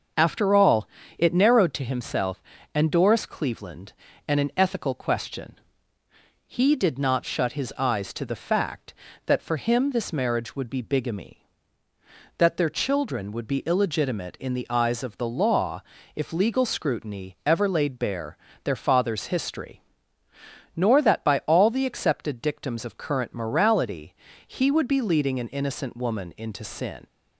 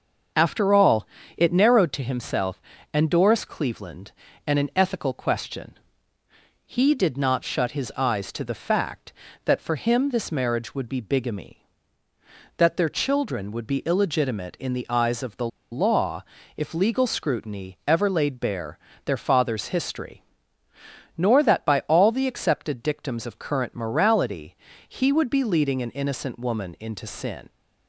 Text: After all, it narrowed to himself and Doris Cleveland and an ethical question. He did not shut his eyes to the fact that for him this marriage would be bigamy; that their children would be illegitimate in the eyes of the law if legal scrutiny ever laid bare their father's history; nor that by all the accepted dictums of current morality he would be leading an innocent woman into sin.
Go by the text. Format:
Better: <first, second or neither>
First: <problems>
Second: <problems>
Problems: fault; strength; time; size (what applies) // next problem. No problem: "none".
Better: first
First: starts louder than the rest; until 1.4 s; 6 dB // pauses between "law" and "if"; slight; at 15.8 s; 0.32 s long // pauses between "bare" and "their"; slight; at 18.3 s; 0.28 s long // pauses between "morality" and "he"; slight; at 24.1 s; 0.32 s long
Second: starts louder than the rest; until 1.6 s; 6 dB // pauses between "the" and "law"; slight; at 15.4 s; 0.24 s long // pauses between "law" and "if"; slight; at 16.2 s; 0.32 s long // pauses between "bare" and "their"; slight; at 18.7 s; 0.28 s long // pauses between "morality" and "he"; slight; at 24.5 s; 0.32 s long